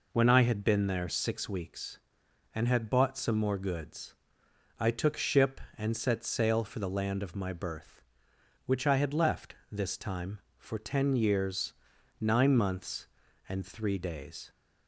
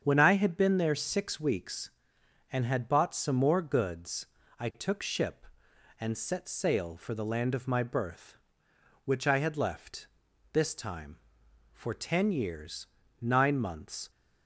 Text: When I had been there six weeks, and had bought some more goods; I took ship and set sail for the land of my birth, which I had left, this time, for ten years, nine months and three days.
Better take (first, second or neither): first